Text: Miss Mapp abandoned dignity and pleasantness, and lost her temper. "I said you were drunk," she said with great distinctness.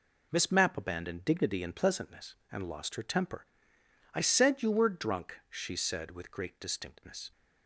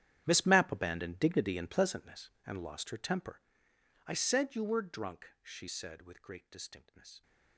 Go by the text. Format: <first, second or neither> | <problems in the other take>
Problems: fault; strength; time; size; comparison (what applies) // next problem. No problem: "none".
first | gets quieter; strong; throughout; 17.5 dB